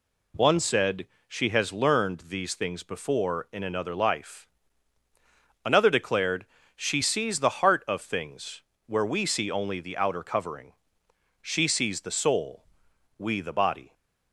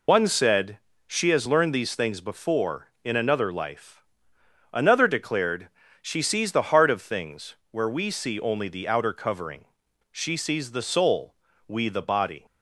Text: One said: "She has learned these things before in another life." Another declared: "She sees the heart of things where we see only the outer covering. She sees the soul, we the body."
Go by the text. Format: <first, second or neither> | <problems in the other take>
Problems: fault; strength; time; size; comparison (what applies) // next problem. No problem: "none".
first | loses the start of "One"; at 0.0 s; 80 ms // pauses between "things" and "where"; slight; at 7.5 s; 0.16 s long; slight in the first